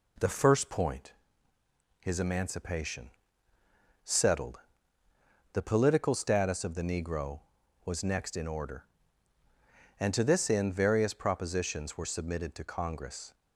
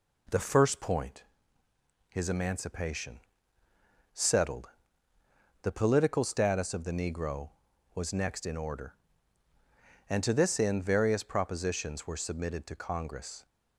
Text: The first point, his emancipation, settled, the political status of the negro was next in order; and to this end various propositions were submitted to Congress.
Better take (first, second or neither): neither